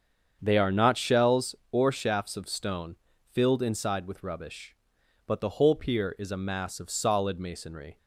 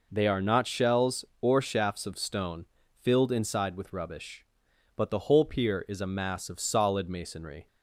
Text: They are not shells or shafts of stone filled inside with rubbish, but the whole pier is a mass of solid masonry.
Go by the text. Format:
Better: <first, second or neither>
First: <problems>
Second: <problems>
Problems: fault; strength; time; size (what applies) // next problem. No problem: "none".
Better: second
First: starts louder than the rest; strong; until 1.5 s; 7.5 dB // pauses between "stone" and "filled"; at 2.9 s; 0.38 s long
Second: pauses between "stone" and "filled"; at 2.6 s; 0.38 s long